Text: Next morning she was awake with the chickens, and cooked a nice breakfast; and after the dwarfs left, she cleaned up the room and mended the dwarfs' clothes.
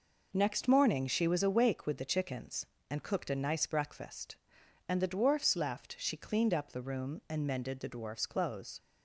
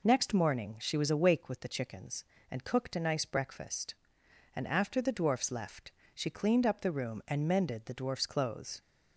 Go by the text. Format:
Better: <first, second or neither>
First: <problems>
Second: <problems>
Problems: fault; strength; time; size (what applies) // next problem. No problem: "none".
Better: second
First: skips "after"; at 5.0 s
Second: none